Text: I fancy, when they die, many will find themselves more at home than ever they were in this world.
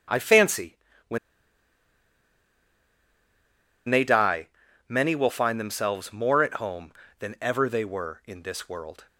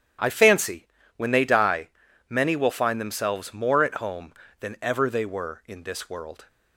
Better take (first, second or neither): second